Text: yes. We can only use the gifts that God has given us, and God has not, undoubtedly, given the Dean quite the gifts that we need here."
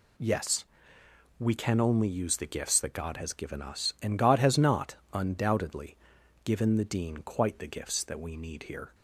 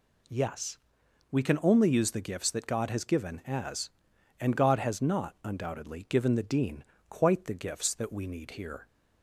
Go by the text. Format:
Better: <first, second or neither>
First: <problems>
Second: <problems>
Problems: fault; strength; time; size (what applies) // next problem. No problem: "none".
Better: first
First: none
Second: says "as" for "us"; at 3.4 s // pauses between "Dean" and "quite"; slight; at 6.8 s; 0.26 s long